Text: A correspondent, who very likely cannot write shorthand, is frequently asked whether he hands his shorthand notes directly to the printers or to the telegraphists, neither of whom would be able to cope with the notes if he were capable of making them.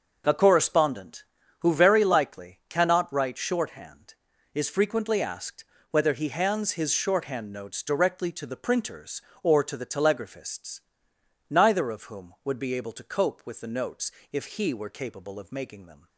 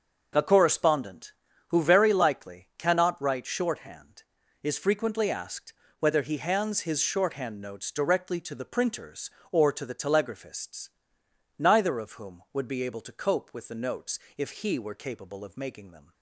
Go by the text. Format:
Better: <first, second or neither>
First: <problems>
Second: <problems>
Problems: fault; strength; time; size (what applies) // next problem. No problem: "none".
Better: neither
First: pauses between "asked" and "whether"; slight; at 5.6 s; 0.28 s long // pauses between "notes" and "if"; slight; at 14.0 s; 0.21 s long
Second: pauses between "asked" and "whether"; slight; at 5.7 s; 0.28 s long // pauses between "notes" and "if"; slight; at 14.1 s; 0.18 s long